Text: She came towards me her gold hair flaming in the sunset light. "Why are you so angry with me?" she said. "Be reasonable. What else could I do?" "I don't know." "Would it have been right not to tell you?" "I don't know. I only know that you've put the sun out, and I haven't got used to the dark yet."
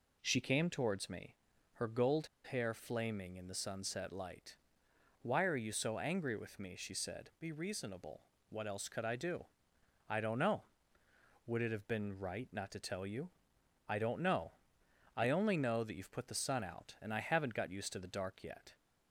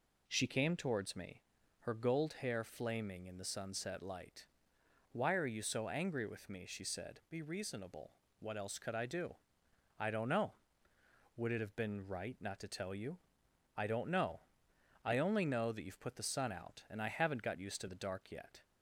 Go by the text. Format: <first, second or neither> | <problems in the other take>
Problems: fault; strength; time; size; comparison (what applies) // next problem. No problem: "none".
second | pauses between "me" and "her"; at 1.3 s; 0.40 s long; also in the second // pauses between "gold" and "hair"; slight; at 2.2 s; 0.24 s long